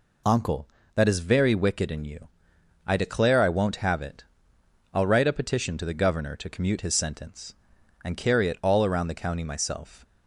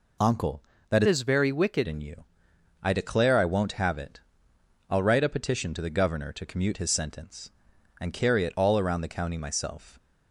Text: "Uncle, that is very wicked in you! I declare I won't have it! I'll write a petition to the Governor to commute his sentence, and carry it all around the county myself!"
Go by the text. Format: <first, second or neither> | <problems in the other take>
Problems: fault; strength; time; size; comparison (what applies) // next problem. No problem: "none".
first | changes voice from "is" to "wicked"; from 1.0 to 1.8 s; 0.8 s long